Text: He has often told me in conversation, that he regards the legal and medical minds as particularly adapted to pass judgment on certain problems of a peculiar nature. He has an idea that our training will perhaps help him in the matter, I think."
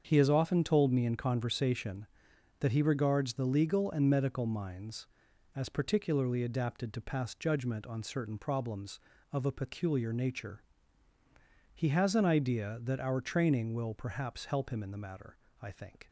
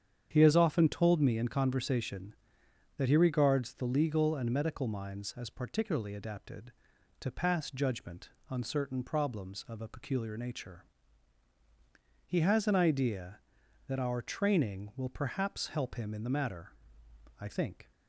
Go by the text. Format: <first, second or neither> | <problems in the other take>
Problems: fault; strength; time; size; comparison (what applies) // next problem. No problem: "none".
neither | starts louder than the rest; the same in both